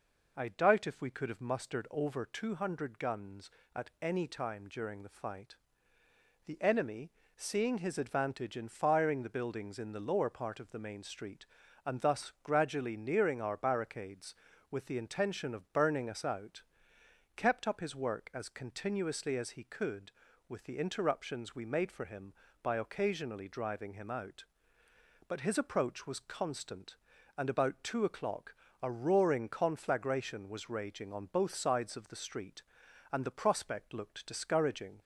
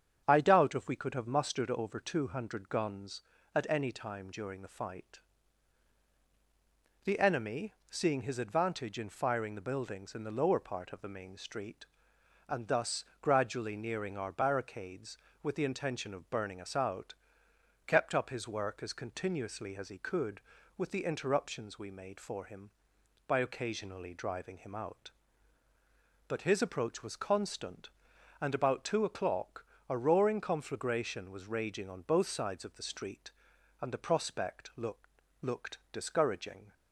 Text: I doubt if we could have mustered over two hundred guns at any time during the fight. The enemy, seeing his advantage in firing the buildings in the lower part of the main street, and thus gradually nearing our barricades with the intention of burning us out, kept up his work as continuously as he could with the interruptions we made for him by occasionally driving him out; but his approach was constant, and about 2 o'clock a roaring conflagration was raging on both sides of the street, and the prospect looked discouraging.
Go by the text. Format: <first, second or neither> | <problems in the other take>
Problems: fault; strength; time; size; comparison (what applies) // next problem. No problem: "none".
first | starts louder than the rest; strong; until 1.2 s; 7.5 dB // pauses between "thus" and "gradually"; slight; at 13.0 s; 0.18 s long // pauses between "o'clock" and "a"; slight; at 29.6 s; 0.24 s long; slight in the first // says "looked" twice; at 35.4 s